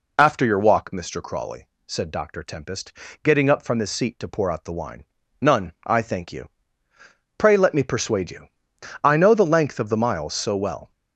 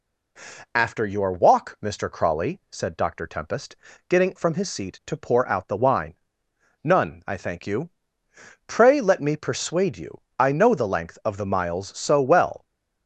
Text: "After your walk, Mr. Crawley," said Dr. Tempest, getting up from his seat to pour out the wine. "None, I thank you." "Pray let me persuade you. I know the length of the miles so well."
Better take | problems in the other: first | skips "up"; at 4.3 s

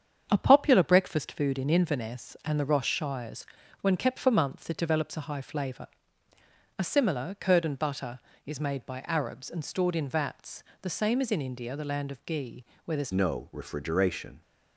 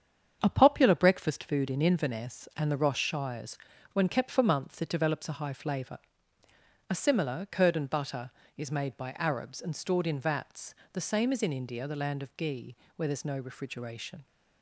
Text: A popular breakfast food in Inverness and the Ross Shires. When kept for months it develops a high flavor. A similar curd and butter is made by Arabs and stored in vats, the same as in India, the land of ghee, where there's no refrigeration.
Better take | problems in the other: second | starts louder than the rest; strong; until 1.2 s; 8 dB; strong in the second // changes voice at "no"; from 13.1 s on; 1.3 s long

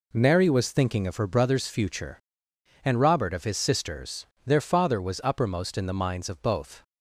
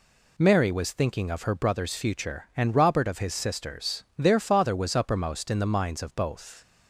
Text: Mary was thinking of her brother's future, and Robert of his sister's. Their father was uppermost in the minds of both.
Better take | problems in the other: neither | none

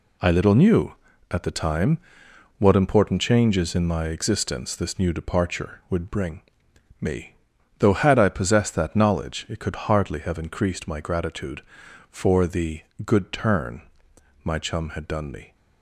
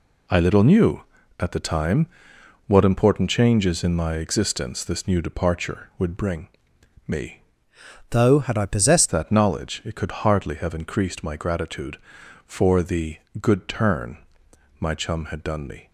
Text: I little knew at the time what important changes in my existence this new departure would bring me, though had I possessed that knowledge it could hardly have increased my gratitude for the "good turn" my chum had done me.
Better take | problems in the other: first | pauses between "time" and "what"; noticeable; at 2.0 s; 0.60 s long; noticeable in the first // pauses between "bring" and "me"; noticeable; at 6.4 s; 0.58 s long; noticeable in the first // changes voice from "though" to "possessed"; from 8.1 to 9.0 s; 0.9 s long // pauses between "the" and "good"; slight; at 13.1 s; 0.24 s long; slight in the first // pauses between "turn" and "my"; noticeable; at 14.1 s; 0.64 s long; noticeable in the first

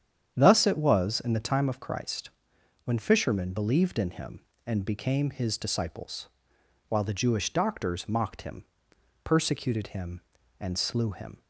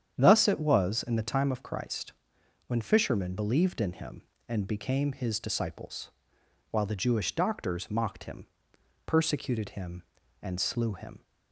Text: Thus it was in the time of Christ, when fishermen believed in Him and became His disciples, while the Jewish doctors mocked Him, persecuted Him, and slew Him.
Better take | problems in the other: neither | starts louder than the rest; strong; the same in both

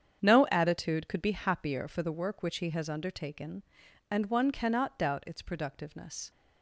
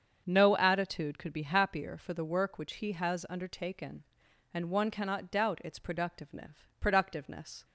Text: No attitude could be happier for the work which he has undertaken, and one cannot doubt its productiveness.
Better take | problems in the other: first | starts louder than the rest; strong; until 1.2 s; 7 dB; strong in the first // says "productiveness" twice; at 6.7 s

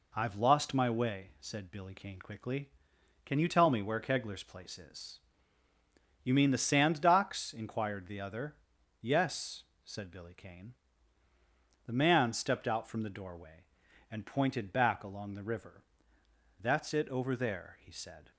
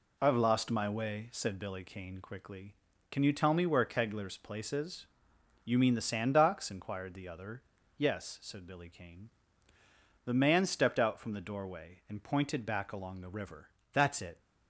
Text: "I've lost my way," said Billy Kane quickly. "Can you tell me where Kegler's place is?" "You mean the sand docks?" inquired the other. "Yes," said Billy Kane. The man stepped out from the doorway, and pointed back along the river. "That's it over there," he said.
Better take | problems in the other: first | stops before "over there he said"; at 14.4 s

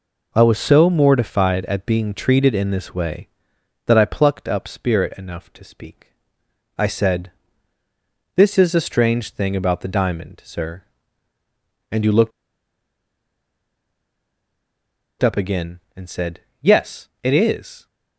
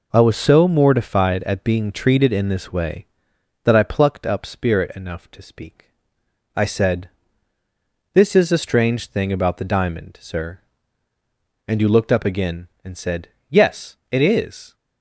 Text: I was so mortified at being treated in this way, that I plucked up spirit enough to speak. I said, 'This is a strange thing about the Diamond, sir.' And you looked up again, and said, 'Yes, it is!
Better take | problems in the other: second | pauses between "looked" and "up"; strong; at 12.3 s; 2.9 s long

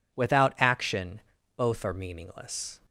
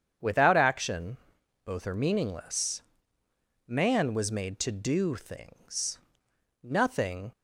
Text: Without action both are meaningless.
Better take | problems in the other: first | starts louder than the rest; strong; until 1.7 s; 8 dB // pauses between "action" and "both"; noticeable; at 1.1 s; 0.48 s long; slight in the first // goes on to say "Man was made to do things Nothing"; strong; from 3.6 s on; 3.6 s long

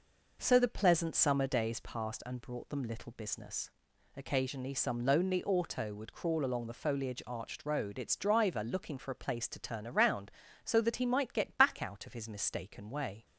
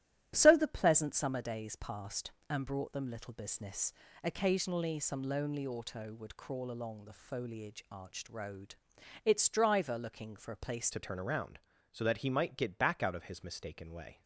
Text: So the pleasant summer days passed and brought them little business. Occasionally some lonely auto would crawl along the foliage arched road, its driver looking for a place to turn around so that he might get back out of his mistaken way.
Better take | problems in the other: first | starts louder than the rest; strong; until 1.3 s; 12 dB // changes voice at "to"; from 10.9 s on; 3.3 s long

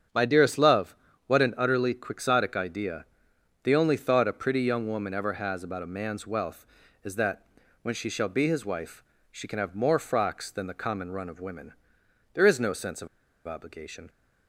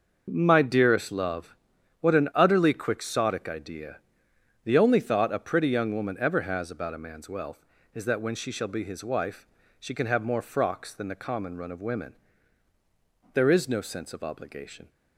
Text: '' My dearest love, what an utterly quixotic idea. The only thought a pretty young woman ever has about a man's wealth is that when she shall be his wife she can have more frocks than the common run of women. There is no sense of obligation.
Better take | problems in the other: second | starts louder than the rest; strong; until 1.4 s; 8 dB; noticeable in the second // pauses between "that" and "when"; at 7.4 s; 0.38 s long // pauses between "wife" and "she"; slight; at 9.0 s; 0.26 s long; slight in the second // pauses between "of" and "obligation"; at 13.0 s; 0.39 s long

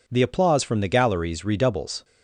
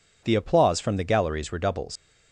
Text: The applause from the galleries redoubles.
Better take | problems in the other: first | leaves "redoubles" unfinished; at 1.9 s; 125 ms

